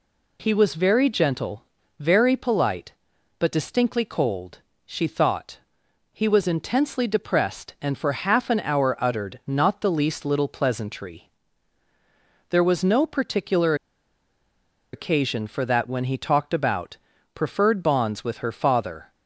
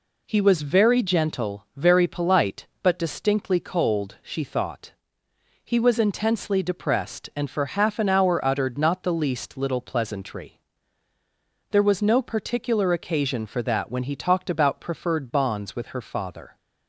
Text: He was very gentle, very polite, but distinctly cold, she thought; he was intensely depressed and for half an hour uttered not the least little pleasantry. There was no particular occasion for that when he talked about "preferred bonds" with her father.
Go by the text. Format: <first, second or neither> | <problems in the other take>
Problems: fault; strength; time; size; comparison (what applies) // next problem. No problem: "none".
second | pauses between "particular" and "occasion"; at 13.7 s; 1.1 s long // pauses between "about" and "preferred"; slight; at 16.9 s; 0.34 s long